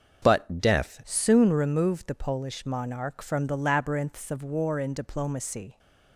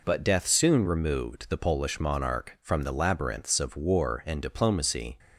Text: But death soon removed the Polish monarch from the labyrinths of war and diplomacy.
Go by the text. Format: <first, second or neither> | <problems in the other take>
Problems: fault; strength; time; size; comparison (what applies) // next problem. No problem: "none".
second | starts louder than the rest; noticeable; until 1.2 s; 6 dB // changes voice at "soon"; from 1.0 s on; 4.7 s long